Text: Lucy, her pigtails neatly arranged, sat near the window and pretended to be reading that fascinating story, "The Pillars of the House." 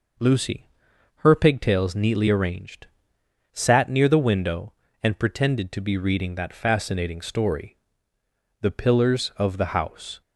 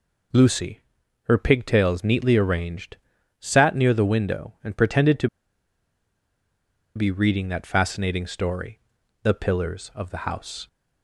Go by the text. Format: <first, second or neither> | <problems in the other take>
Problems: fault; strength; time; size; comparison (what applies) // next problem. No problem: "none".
first | pauses between "to" and "be"; strong; at 5.2 s; 1.6 s long